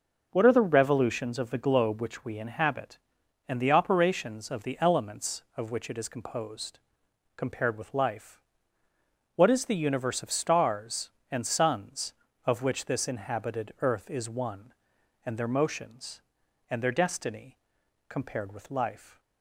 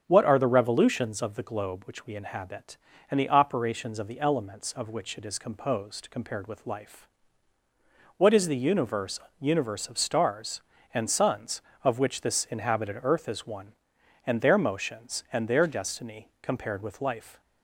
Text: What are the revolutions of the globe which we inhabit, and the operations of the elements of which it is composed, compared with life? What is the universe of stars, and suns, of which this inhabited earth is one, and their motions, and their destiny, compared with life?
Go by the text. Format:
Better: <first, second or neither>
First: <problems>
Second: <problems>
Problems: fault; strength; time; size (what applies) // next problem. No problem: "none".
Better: first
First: none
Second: starts louder than the rest; strong; until 1.0 s; 8 dB // says "universe" twice; at 9.3 s